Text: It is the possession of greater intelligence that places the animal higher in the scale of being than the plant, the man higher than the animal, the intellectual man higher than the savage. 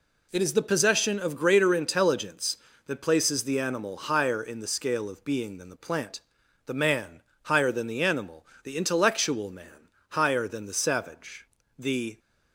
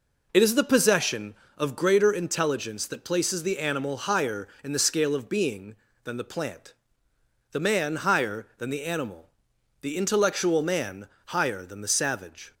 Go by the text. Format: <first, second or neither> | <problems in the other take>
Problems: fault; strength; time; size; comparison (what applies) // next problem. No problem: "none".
second | pauses between "man" and "higher"; slight; at 7.2 s; 0.22 s long // pauses between "man" and "higher"; slight; at 9.8 s; 0.22 s long; slight in the second // goes on to say "The"; slight; from 11.7 s on; 0.42 s long